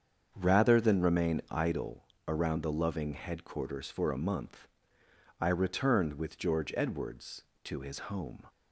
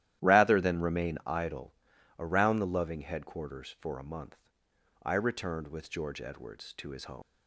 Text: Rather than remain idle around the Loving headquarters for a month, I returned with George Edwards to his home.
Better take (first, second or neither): first